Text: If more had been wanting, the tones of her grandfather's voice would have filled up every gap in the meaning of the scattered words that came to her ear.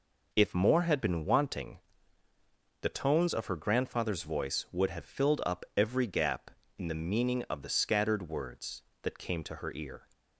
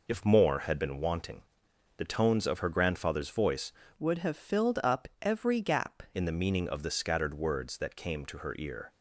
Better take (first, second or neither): first